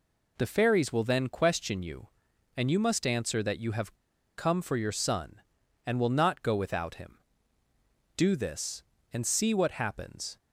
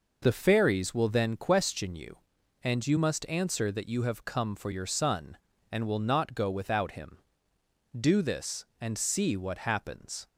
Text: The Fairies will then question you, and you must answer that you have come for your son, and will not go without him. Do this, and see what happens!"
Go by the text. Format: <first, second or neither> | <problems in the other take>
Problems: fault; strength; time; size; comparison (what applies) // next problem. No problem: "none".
second | pauses between "have" and "come"; at 3.9 s; 0.41 s long